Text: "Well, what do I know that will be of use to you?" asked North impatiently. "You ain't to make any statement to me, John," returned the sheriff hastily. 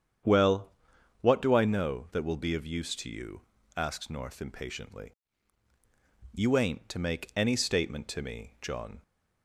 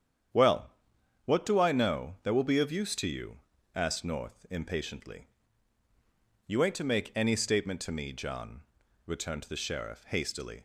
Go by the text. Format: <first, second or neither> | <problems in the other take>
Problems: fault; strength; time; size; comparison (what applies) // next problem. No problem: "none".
second | starts louder than the rest; strong; until 1.7 s; 8.5 dB; strong in the second // stops before "returned the sheriff hastily"; at 9.0 s